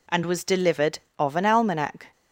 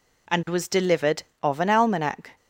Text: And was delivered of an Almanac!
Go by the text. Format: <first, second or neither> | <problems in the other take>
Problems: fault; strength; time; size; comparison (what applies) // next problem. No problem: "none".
neither | none